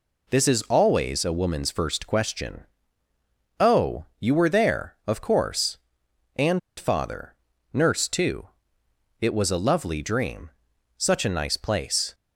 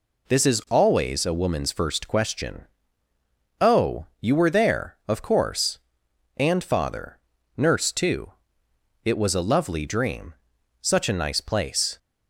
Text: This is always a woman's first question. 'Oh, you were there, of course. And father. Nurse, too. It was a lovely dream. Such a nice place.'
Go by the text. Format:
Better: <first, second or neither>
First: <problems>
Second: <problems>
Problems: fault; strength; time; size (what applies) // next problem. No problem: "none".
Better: second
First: pauses between "And" and "father"; slight; at 6.5 s; 0.18 s long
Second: none